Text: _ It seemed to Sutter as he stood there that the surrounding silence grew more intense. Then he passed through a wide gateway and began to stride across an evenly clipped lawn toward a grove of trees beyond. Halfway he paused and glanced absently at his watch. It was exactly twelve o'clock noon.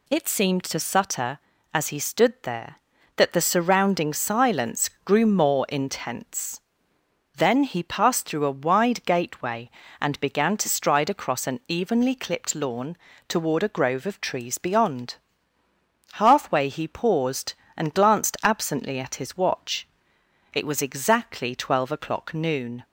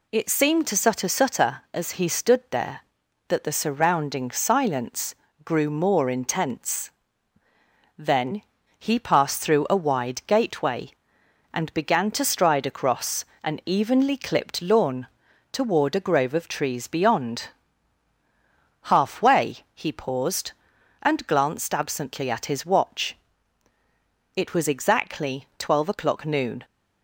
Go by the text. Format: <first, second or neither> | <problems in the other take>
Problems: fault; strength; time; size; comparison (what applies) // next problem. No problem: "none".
first | says "Sutter" twice; at 1.0 s // pauses between "silence" and "grew"; slight; at 5.1 s; 0.30 s long; slight in the first // pauses between "Then" and "he"; at 8.4 s; 0.38 s long // pauses between "across" and "an"; slight; at 13.2 s; 0.18 s long // pauses between "lawn" and "toward"; at 15.0 s; 0.44 s long; slight in the first // pauses between "Halfway" and "he"; slight; at 19.5 s; 0.16 s long